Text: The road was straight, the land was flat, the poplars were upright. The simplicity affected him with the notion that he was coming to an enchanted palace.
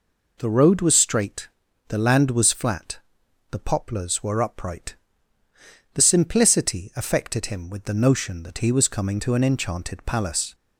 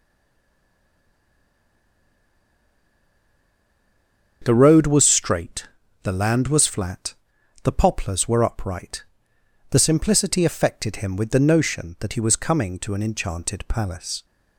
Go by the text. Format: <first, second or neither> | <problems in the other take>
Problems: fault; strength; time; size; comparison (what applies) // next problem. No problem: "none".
first | stays silent before the first word; strong; until 4.4 s; 4.4 s long // starts louder than the rest; until 5.4 s; 7 dB